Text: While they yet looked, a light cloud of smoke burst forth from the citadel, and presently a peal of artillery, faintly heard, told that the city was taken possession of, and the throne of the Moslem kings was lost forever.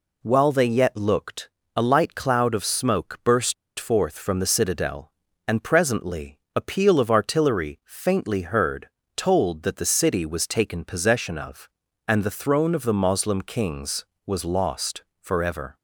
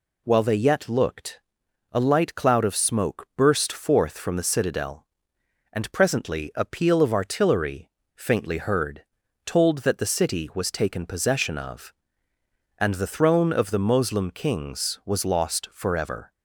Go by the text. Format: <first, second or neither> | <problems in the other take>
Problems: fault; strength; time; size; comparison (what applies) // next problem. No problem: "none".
second | pauses between "burst" and "forth"; slight; at 3.5 s; 0.24 s long // pauses between "presently" and "a"; slight; at 6.3 s; 0.16 s long // pauses between "lost" and "forever"; slight; at 15.0 s; 0.16 s long